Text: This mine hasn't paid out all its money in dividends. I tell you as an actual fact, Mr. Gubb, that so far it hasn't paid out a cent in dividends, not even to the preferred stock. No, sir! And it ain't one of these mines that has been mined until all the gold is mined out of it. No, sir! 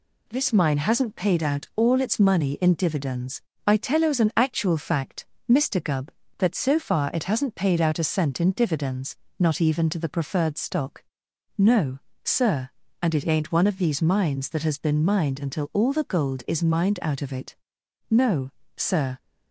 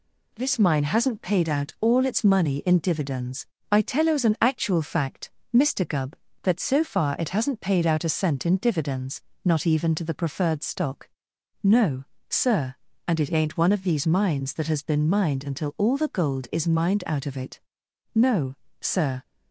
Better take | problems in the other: neither | none

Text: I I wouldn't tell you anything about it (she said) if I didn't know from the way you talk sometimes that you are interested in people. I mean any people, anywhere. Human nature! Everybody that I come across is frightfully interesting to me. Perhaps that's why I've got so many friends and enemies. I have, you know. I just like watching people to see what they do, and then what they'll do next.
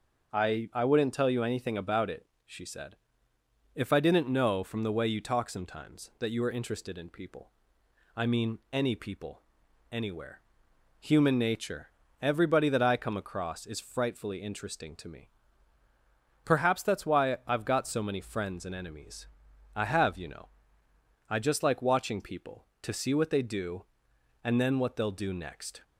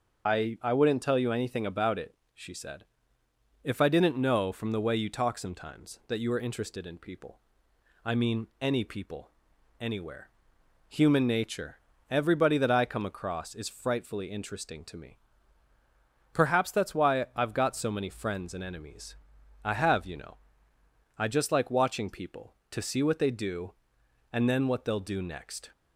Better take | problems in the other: first | loses the start of "I"; at 0.2 s; 45 ms

